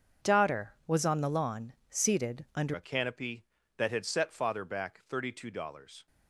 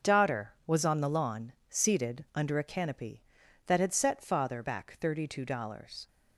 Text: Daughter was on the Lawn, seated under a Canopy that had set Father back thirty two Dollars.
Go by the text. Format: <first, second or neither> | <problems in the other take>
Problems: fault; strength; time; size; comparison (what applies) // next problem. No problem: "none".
second | starts louder than the rest; until 1.3 s; 7 dB; also in the second // changes voice at "a"; from 2.7 s on; 3.3 s long